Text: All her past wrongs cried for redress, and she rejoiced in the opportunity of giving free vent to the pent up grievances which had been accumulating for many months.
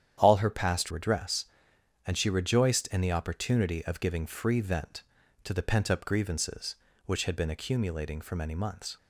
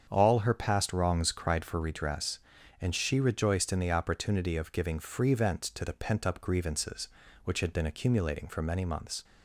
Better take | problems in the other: second | starts louder than the rest; strong; until 1.1 s; 9.5 dB; strong in the second // skips "wrongs cried for"; at 0.9 s

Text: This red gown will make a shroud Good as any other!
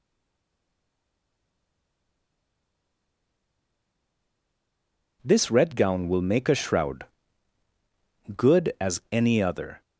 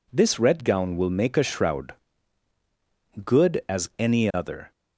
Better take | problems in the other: second | stays silent before the first word; strong; until 5.2 s; 5.2 s long // pauses between "shroud" and "Good"; strong; at 7.0 s; 1.3 s long; strong in the second

